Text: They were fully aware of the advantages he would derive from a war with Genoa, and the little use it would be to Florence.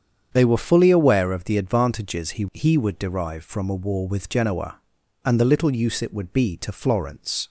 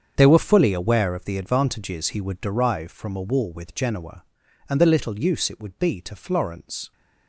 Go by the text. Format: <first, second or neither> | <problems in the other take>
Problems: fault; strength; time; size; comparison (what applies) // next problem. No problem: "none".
second | starts louder than the rest; strong; until 1.3 s; 8 dB; strong in the second // says "he" twice; at 2.5 s